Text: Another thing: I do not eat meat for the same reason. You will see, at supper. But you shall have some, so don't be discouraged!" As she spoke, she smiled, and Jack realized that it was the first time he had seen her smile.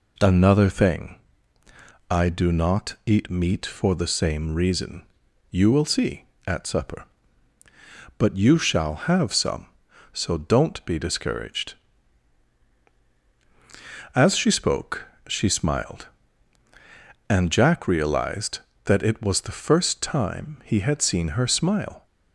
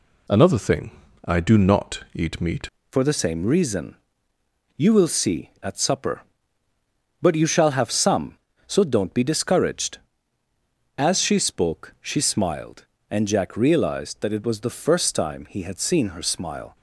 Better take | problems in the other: first | changes voice at "for"; from 2.9 s on; 13.8 s long

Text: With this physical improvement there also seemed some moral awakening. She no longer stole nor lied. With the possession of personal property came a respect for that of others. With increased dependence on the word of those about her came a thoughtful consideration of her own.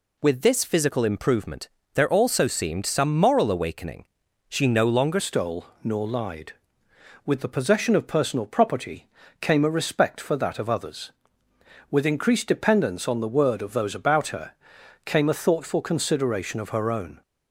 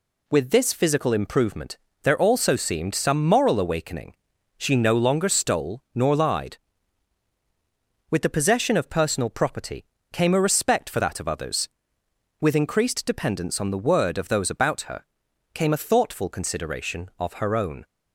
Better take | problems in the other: second | pauses between "improvement" and "there"; slight; at 1.6 s; 0.26 s long; slight in the second // changes voice at "stole"; from 5.1 s on; 12.1 s long // pauses between "stole" and "nor"; slight; at 5.6 s; 0.18 s long // pauses between "property" and "came"; slight; at 9.0 s; 0.34 s long; slight in the second // pauses between "her" and "came"; noticeable; at 14.5 s; 0.52 s long; noticeable in the second

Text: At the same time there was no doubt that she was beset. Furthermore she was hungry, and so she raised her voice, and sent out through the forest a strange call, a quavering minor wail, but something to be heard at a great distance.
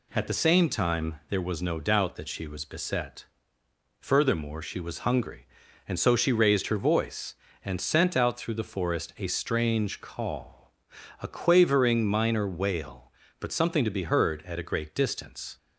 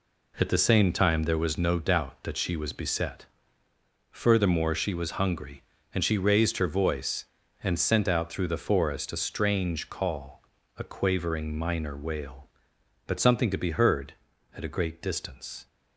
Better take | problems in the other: first | skips "so"; at 6.0 s

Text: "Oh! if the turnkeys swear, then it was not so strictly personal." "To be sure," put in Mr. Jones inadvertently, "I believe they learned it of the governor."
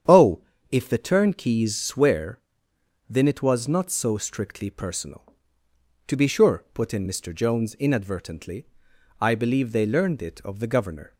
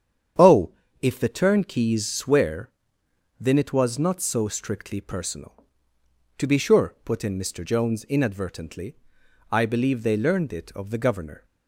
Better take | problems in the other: neither | starts louder than the rest; strong; the same in both

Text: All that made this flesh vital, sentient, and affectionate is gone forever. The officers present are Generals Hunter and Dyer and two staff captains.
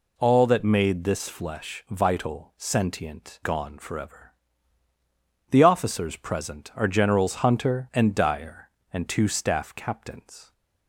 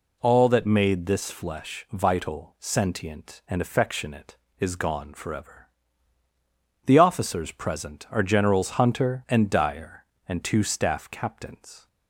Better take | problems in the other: second | skips "and affectionate is"; at 3.4 s

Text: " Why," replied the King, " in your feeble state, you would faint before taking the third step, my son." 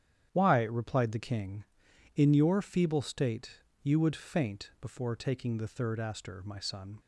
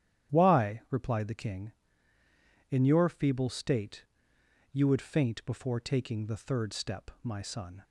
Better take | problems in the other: second | starts louder than the rest; strong; until 1.3 s; 9 dB; strong in the second // says "aster" for "step"; at 5.9 s

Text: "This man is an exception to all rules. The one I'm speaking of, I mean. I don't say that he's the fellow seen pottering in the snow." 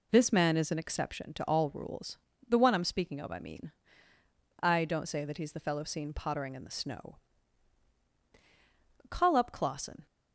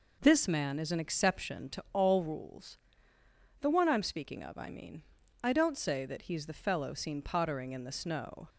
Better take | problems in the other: second | goes on to say "Call up Clausen"; noticeable; from 9.1 s on; 0.94 s long

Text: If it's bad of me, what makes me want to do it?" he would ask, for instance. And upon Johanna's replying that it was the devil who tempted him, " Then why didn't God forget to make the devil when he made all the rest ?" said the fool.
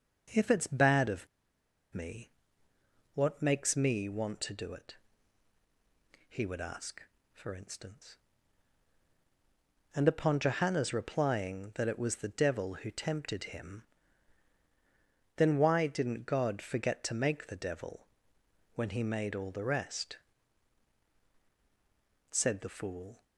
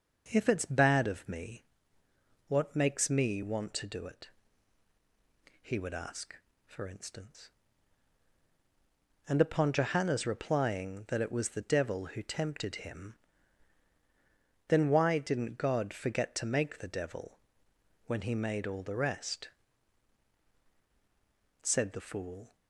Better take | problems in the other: second | pauses between "of" and "me"; noticeable; at 1.2 s; 0.67 s long // pauses between "devil" and "when"; noticeable; at 18.0 s; 0.70 s long; noticeable in the second

